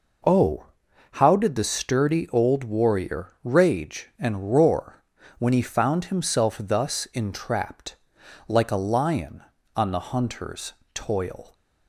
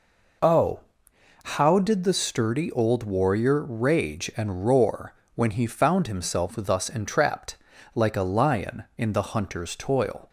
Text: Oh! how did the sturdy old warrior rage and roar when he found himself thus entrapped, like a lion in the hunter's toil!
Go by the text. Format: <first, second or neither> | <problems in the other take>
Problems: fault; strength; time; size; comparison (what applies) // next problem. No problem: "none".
second | pauses between "roar" and "when"; slight; at 5.0 s; 0.34 s long; slight in the second // says "on" for "in"; at 9.7 s // pauses between "hunter's" and "toil"; slight; at 10.7 s; 0.20 s long